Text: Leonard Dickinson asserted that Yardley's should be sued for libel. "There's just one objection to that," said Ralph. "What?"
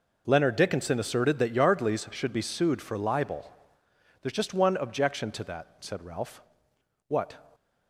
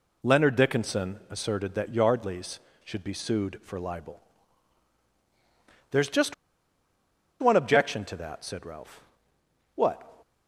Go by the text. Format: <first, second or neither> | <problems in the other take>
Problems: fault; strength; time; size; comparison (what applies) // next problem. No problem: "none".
first | pauses between "just" and "one"; at 6.3 s; 1.0 s long